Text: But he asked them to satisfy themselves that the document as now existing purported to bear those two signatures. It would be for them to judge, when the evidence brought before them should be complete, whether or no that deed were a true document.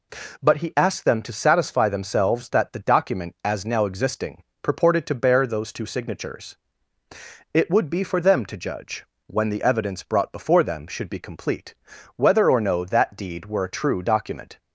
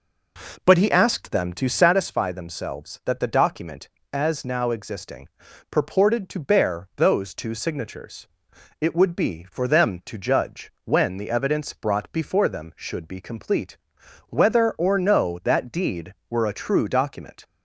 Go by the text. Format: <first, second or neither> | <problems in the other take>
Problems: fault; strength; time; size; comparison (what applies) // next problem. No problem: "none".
first | starts louder than the rest; noticeable; until 2.0 s; 4.5 dB // pauses between "existing" and "purported"; at 5.2 s; 0.42 s long; slight in the first